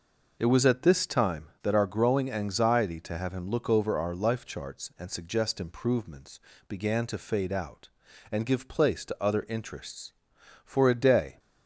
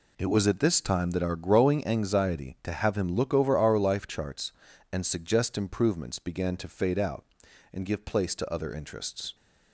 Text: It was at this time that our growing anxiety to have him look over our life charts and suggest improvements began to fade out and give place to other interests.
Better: second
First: pauses between "improvements" and "began"; slight; at 6.3 s; 0.30 s long // goes on to say "For a day"; noticeable; from 10.6 s on; 0.74 s long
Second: none

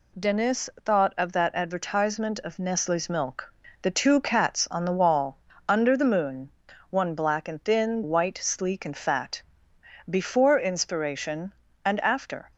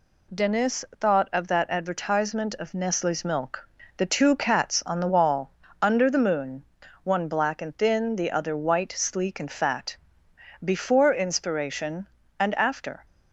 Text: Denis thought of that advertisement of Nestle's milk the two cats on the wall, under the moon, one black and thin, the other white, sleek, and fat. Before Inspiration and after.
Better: second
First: pauses between "Denis" and "thought"; slight; at 0.6 s; 0.16 s long // pauses between "milk" and "the"; slight; at 3.4 s; 0.30 s long // skips "the other"; at 8.0 s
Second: pauses between "Denis" and "thought"; slight; at 0.8 s; 0.16 s long // pauses between "milk" and "the"; slight; at 3.6 s; 0.30 s long

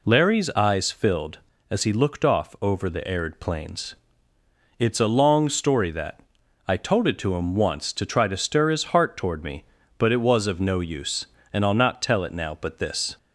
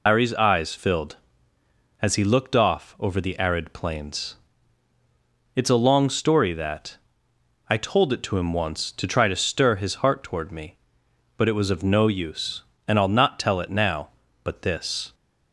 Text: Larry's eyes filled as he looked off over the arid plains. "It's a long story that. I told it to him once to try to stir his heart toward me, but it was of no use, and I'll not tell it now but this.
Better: first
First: none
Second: loses the start of "Larry's"; at 0.0 s; 125 ms

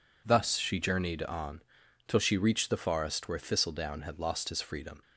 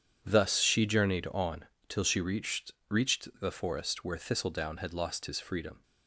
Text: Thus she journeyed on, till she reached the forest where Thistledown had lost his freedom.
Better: first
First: none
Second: says "reached" twice; at 2.8 s

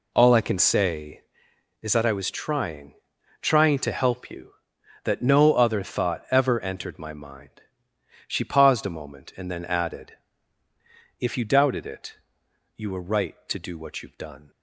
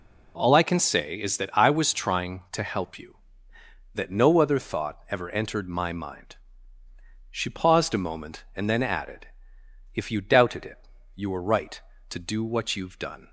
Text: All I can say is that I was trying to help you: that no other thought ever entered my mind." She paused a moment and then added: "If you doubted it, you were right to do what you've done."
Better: second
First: says "trying" twice; at 3.4 s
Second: none

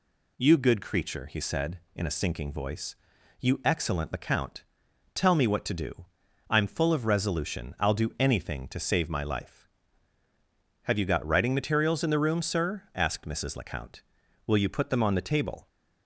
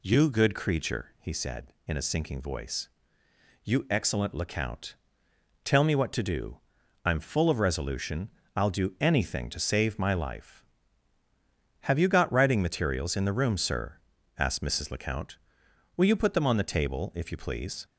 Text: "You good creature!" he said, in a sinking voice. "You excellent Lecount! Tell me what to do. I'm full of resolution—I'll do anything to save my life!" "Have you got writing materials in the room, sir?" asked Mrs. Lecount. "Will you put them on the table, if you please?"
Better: second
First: stops before "if you please"; at 15.6 s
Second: none

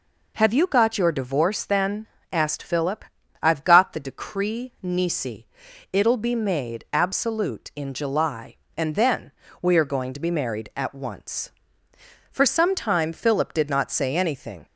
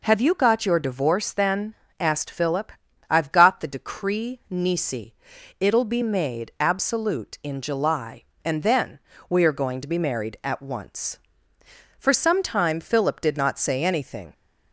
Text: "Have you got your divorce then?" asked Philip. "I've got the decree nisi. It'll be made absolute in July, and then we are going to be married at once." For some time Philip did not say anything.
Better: neither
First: pauses between "then" and "we"; slight; at 9.3 s; 0.30 s long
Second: pauses between "then" and "we"; slight; at 8.9 s; 0.30 s long

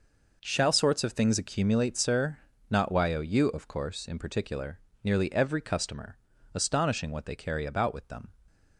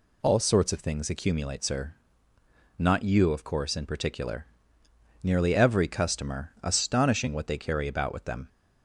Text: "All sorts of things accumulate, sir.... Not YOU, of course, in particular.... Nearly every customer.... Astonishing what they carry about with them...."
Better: second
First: says "Shall" for "All"; at 0.4 s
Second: none

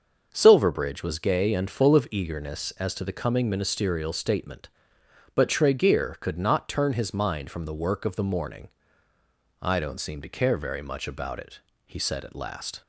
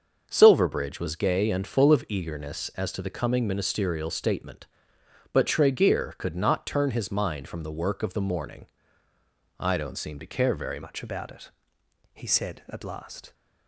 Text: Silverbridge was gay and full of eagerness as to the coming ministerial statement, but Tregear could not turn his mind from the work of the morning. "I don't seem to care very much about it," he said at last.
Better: first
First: starts louder than the rest; until 1.3 s; 6.5 dB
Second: starts louder than the rest; until 1.2 s; 6.5 dB // changes voice at "much"; from 10.8 s on; 2.5 s long

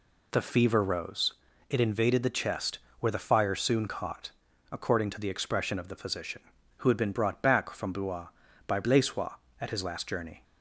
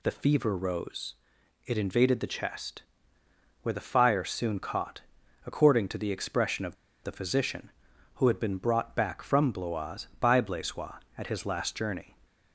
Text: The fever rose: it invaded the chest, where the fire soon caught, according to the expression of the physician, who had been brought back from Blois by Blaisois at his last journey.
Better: first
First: none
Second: pauses between "of" and "the"; slight; at 6.7 s; 0.29 s long

